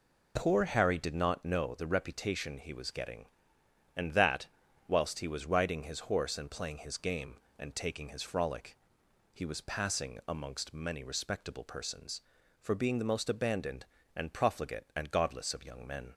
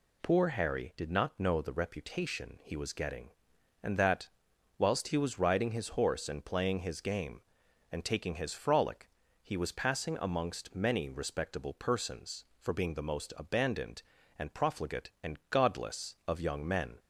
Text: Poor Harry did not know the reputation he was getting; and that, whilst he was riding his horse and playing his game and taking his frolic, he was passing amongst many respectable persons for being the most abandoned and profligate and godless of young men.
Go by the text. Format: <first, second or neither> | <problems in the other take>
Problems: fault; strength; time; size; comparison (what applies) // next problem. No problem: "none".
neither | none